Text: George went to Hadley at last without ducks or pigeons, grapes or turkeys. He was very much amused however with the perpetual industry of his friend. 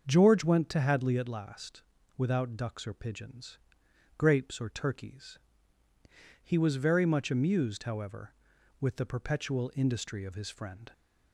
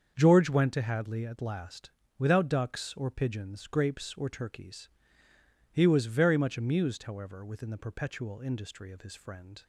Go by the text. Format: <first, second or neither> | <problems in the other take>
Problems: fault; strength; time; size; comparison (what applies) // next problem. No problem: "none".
first | starts louder than the rest; until 1.1 s; 7 dB; also in the first // pauses between "last" and "without"; slight; at 1.8 s; 0.28 s long; also in the first // says "within" for "with"; at 7.4 s